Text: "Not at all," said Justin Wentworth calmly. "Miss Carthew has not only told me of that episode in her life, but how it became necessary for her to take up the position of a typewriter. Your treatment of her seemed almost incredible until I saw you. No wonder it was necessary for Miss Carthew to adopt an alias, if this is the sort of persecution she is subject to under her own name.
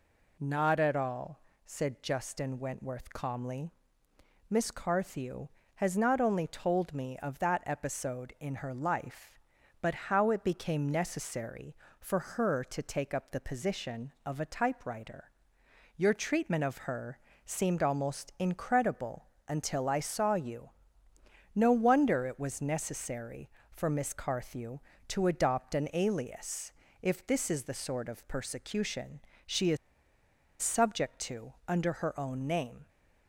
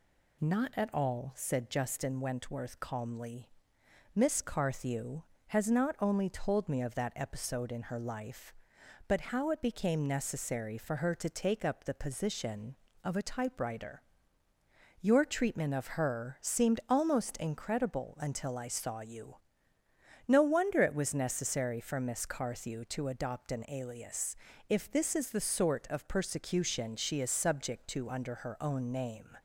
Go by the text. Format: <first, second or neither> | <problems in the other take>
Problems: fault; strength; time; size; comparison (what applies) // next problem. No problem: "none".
second | pauses between "her" and "seemed"; slight; at 17.1 s; 0.28 s long // pauses between "incredible" and "until"; slight; at 19.2 s; 0.20 s long // pauses between "persecution" and "she"; slight; at 29.1 s; 0.26 s long // pauses between "is" and "subject"; noticeable; at 29.7 s; 0.84 s long